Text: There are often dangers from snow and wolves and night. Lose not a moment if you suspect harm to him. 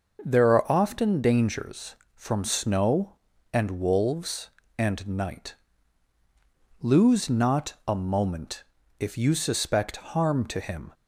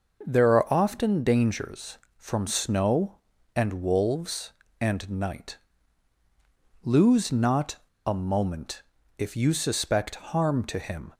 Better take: first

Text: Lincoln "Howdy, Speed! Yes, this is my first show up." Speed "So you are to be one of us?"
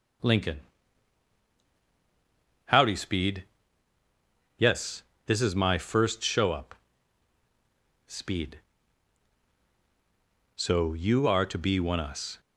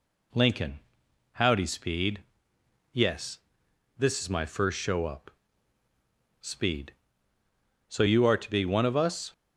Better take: second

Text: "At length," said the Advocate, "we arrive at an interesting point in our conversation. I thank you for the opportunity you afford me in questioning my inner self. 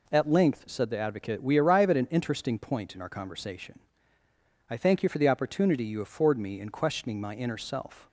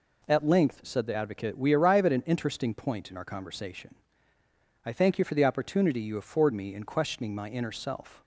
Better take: neither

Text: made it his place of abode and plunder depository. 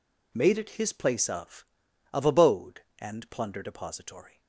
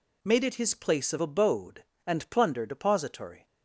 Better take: second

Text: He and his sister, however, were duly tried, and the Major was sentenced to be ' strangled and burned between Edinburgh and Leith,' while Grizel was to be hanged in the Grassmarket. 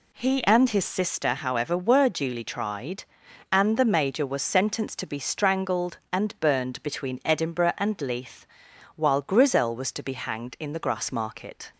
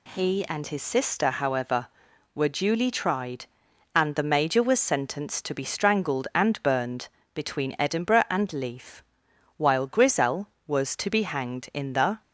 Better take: first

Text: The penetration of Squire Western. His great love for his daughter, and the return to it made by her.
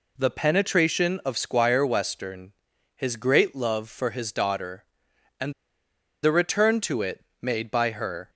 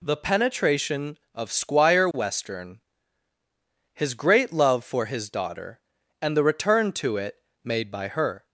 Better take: second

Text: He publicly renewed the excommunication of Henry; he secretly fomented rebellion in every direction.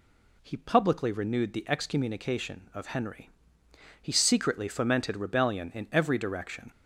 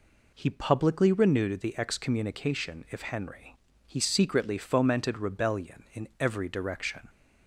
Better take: first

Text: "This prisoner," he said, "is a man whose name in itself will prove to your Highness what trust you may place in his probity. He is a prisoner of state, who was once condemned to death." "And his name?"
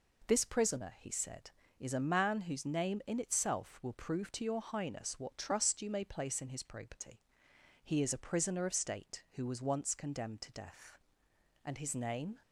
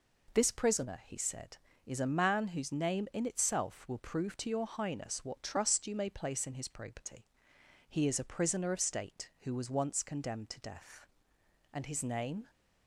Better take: neither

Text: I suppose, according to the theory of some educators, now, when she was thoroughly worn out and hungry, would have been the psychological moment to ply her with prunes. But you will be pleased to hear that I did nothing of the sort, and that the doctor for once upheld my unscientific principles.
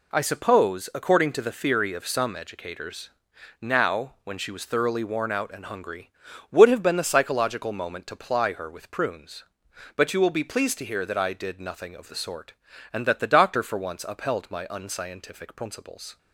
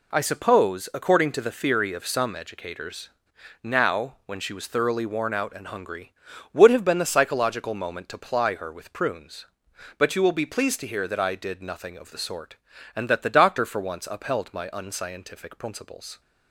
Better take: neither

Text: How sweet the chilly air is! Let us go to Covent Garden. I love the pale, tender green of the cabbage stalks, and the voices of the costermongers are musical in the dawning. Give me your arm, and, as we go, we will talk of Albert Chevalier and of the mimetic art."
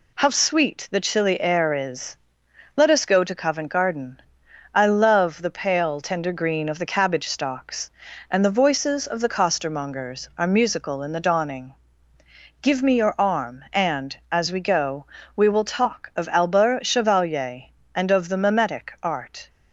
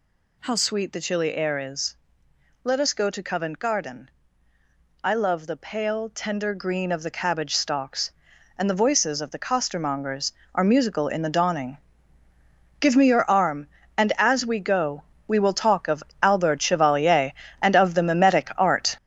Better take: first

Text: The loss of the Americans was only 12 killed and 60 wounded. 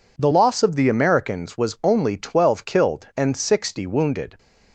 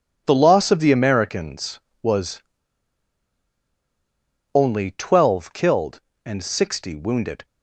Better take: first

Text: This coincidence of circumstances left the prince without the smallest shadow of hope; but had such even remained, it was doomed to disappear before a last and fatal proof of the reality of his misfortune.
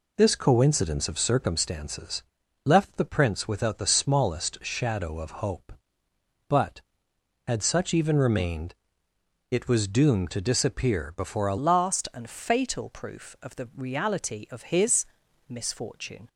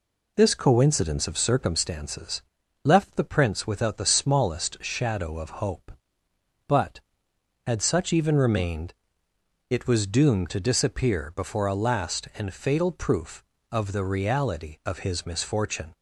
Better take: second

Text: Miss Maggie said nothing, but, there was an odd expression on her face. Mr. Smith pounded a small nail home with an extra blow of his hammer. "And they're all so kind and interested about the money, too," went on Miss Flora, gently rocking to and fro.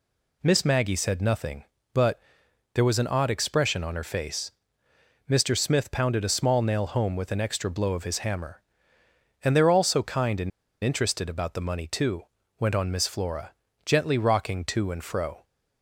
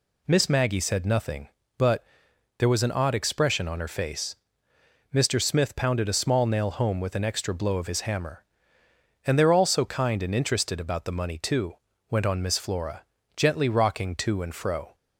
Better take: second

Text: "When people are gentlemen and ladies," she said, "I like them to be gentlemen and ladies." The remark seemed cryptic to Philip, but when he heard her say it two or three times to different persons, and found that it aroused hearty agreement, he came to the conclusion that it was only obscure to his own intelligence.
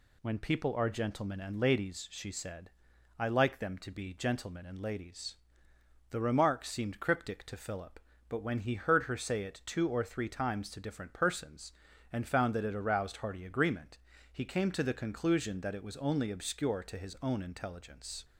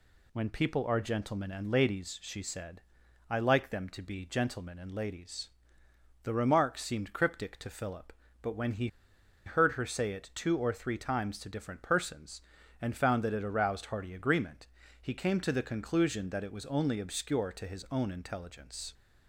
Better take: first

